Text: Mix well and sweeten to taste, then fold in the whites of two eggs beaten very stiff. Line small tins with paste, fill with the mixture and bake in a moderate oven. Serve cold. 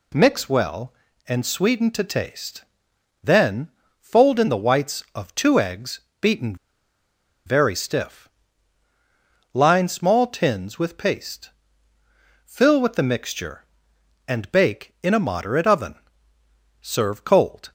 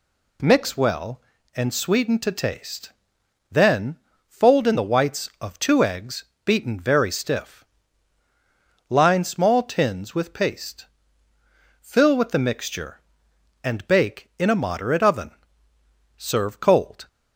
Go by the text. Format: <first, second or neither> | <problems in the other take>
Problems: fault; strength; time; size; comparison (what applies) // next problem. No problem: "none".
second | pauses between "then" and "fold"; slight; at 3.6 s; 0.30 s long; slight in the second // pauses between "eggs" and "beaten"; slight; at 6.0 s; 0.20 s long; slight in the second // pauses between "beaten" and "very"; noticeable; at 6.5 s; 0.90 s long